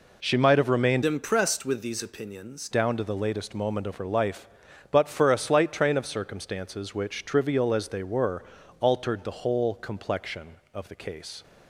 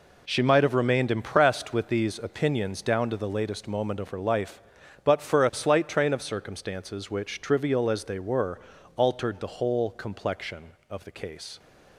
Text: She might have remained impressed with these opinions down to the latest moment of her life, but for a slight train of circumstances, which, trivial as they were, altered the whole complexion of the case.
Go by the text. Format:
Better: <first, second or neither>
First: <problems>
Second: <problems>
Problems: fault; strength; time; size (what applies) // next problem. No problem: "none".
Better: second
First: changes voice from "impressed" to "opinions"; from 1.0 to 2.6 s; 1.6 s long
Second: none